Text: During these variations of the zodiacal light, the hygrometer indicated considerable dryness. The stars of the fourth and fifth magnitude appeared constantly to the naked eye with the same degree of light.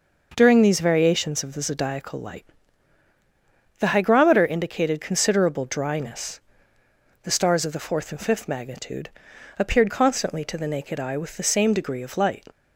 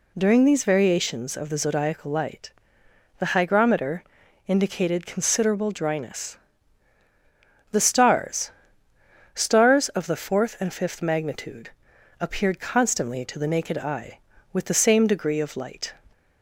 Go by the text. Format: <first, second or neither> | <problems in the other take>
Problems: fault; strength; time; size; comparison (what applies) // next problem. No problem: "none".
first | pauses between "hygrometer" and "indicated"; at 4.0 s; 0.44 s long // says "stars" twice; at 9.3 s // pauses between "magnitude" and "appeared"; noticeable; at 11.6 s; 0.50 s long; noticeable in the first